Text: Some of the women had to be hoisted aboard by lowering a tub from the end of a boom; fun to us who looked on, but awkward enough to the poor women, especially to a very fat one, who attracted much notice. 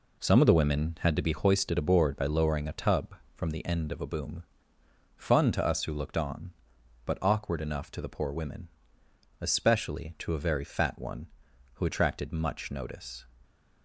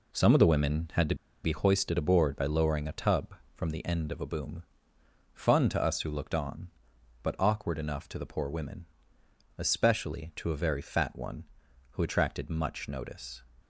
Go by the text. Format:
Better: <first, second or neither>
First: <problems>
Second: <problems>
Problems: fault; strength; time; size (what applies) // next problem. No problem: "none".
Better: first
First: none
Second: pauses between "to" and "be"; slight; at 1.1 s; 0.28 s long